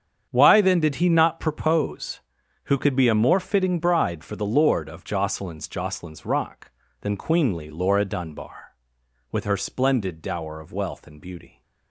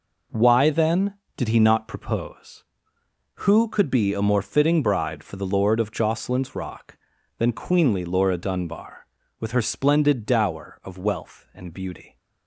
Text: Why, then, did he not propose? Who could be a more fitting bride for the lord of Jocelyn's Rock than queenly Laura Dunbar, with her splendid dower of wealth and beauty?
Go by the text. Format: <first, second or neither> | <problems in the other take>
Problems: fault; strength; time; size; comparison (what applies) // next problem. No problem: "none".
second | starts louder than the rest; strong; until 1.3 s; 8 dB // says "Jocelyn's" twice; at 5.6 s